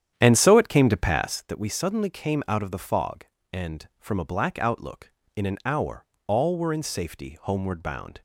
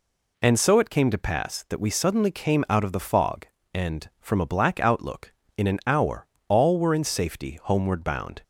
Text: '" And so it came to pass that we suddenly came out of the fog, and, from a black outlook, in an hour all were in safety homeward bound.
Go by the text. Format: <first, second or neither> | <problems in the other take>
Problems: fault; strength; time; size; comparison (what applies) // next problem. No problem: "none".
second | starts louder than the rest; strong; until 1.6 s; 9.5 dB // pauses between "hour" and "all"; slight; at 6.0 s; 0.22 s long; slight in the second